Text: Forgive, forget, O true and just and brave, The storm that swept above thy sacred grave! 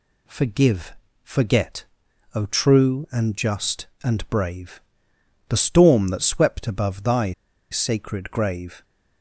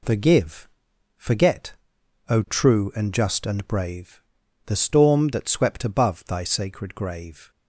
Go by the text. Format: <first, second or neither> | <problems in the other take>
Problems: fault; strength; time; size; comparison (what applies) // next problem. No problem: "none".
second | pauses between "thy" and "sacred"; at 7.3 s; 0.38 s long